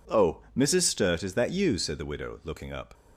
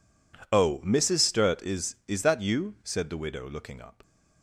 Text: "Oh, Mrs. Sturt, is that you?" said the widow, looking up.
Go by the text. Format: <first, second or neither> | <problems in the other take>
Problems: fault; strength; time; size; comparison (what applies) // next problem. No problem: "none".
first | says "is" twice; at 2.0 s